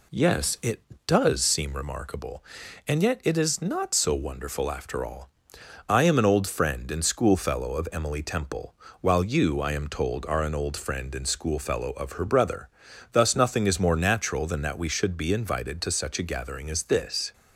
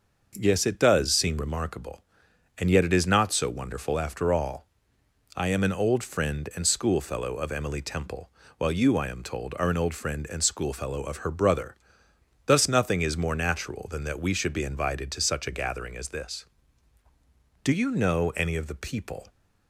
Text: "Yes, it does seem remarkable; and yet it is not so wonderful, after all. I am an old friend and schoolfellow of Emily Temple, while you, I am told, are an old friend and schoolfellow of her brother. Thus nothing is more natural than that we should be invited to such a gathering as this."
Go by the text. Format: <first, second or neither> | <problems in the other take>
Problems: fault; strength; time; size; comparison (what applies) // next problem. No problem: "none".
first | starts louder than the rest; noticeable; until 1.3 s; 6 dB // goes on to say "Do you know any of the people"; from 17.6 s on; 1.6 s long